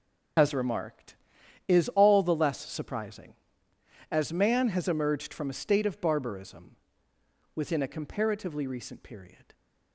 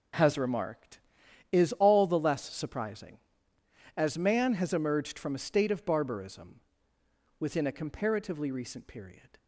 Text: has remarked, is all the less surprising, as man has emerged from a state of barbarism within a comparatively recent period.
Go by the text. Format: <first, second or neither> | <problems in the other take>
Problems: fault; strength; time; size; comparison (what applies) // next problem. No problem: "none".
second | loses the start of "has"; at 0.3 s; 75 ms // pauses between "barbarism" and "within"; noticeable; at 6.7 s; 0.80 s long; noticeable in the second